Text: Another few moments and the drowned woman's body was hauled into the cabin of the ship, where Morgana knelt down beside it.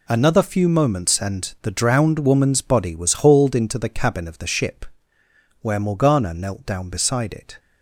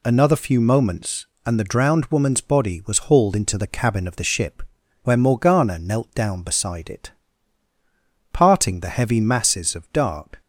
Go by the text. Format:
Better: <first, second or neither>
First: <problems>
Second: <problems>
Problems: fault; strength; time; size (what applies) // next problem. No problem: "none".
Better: first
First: none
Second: goes on to say "Parting the heavy masses of dark"; strong; from 8.3 s on; 2.1 s long